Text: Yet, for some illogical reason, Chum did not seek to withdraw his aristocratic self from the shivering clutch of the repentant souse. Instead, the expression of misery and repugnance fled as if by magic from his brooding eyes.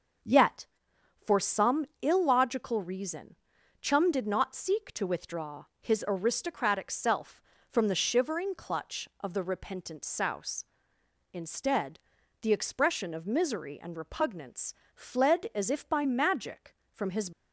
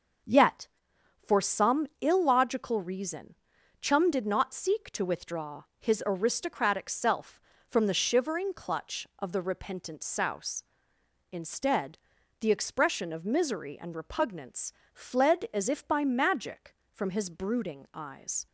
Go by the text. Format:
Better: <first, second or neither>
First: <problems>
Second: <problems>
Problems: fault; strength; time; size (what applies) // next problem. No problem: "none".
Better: second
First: starts louder than the rest; until 1.8 s; 6.5 dB // pauses between "withdraw" and "his"; slight; at 5.6 s; 0.16 s long // pauses between "repugnance" and "fled"; slight; at 14.7 s; 0.20 s long // stops before "brooding eyes"; at 17.3 s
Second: starts louder than the rest; until 1.8 s; 6.5 dB // pauses between "withdraw" and "his"; slight; at 5.6 s; 0.16 s long // pauses between "repugnance" and "fled"; slight; at 14.7 s; 0.20 s long